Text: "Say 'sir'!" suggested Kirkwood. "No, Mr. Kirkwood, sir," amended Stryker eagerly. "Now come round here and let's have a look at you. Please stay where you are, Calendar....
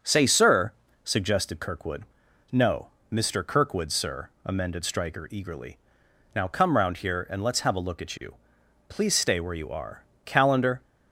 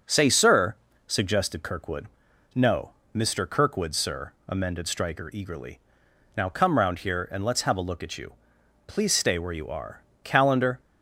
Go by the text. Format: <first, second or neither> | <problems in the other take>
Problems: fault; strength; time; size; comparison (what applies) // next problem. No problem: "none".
neither | none